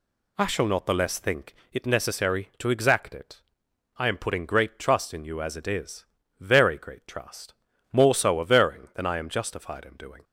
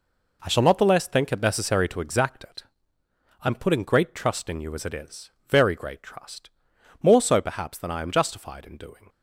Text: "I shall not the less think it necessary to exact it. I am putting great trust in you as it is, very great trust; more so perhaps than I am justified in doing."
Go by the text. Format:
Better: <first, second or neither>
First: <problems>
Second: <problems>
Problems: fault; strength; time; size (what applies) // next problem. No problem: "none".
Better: second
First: pauses between "think" and "it"; slight; at 1.5 s; 0.18 s long // says "averring" for "perhaps"; at 8.4 s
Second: none